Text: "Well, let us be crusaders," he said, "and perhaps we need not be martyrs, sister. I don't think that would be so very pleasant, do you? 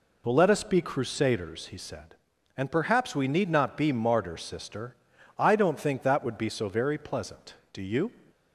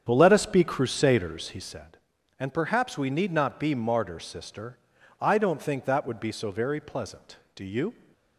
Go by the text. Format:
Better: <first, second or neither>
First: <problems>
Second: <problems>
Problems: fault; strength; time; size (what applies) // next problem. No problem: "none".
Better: first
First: none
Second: starts louder than the rest; strong; until 1.8 s; 8 dB